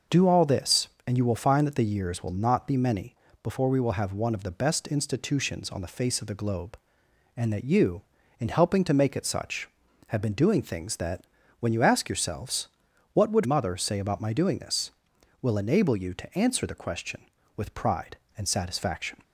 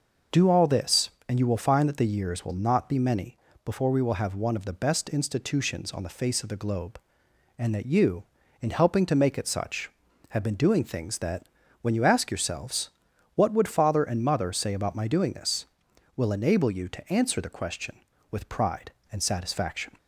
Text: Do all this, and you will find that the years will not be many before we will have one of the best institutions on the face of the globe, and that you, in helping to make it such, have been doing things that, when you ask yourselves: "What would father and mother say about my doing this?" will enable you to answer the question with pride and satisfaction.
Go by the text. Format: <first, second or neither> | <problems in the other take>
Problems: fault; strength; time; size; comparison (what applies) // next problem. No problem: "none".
second | pauses between "many" and "before"; slight; at 3.1 s; 0.28 s long; slight in the second // skips "father and"; at 13.4 s